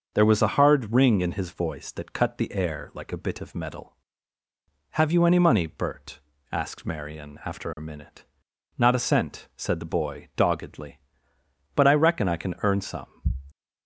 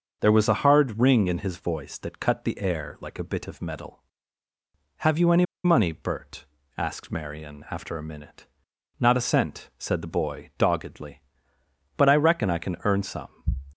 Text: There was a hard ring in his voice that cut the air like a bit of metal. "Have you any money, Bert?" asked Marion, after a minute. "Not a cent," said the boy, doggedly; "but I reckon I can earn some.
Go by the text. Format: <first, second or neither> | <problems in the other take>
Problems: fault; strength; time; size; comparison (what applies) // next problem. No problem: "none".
first | starts louder than the rest; until 1.2 s; 6 dB; also in the first // pauses between "any" and "money"; slight; at 5.4 s; 0.20 s long